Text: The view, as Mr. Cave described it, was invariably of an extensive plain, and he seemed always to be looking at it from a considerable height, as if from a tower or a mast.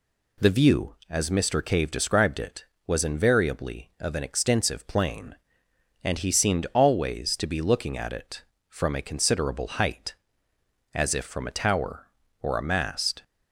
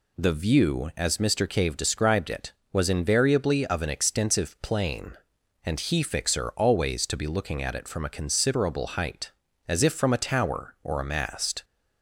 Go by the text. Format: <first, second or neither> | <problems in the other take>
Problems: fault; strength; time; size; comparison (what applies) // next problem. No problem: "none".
first | says "fixer" for "seemed"; at 6.0 s